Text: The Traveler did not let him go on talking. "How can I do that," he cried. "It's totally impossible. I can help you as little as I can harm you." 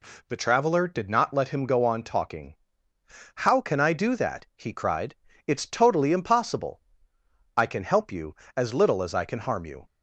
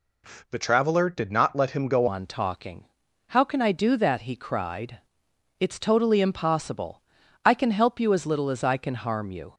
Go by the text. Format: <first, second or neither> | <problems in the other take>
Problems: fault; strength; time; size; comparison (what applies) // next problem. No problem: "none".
first | changes voice at "on"; from 2.0 s on; 7.5 s long